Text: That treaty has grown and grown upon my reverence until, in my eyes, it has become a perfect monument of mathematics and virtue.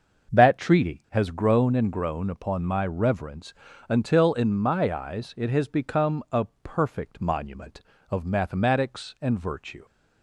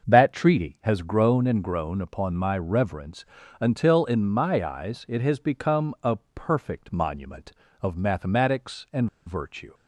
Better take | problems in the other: first | starts louder than the rest; until 1.1 s; 6 dB; also in the first // pauses between "reverence" and "until"; slight; at 3.2 s; 0.34 s long; slight in the first // pauses between "a" and "perfect"; slight; at 6.1 s; 0.18 s long; slight in the first // pauses between "and" and "virtue"; slight; at 9.0 s; 0.18 s long

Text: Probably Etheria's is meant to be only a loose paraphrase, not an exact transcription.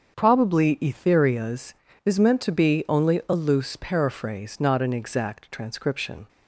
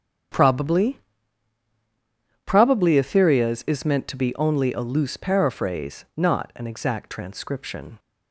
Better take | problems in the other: first | starts louder than the rest; strong; until 2.8 s; 8 dB; also in the first // says "Probably" twice; at 2.4 s

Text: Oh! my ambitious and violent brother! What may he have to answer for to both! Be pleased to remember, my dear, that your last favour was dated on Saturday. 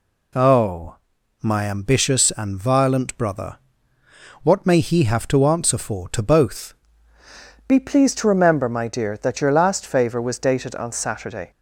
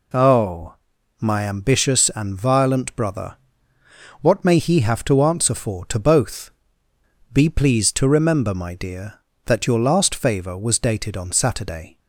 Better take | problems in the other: second | changes voice at "Be"; from 7.6 s on; 3.9 s long

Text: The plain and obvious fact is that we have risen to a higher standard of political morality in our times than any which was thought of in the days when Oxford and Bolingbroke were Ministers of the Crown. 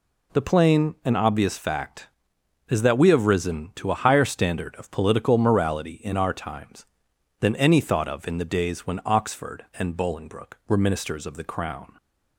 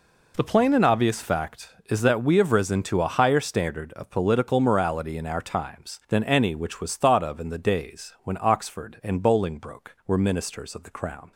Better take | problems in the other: second | skips "which was"; at 7.7 s

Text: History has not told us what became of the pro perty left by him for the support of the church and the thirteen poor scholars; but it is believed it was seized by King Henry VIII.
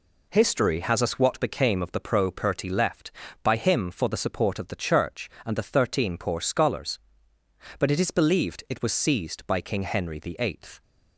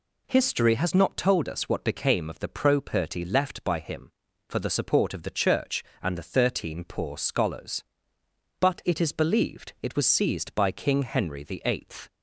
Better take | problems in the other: second | skips "not told"; at 1.0 s

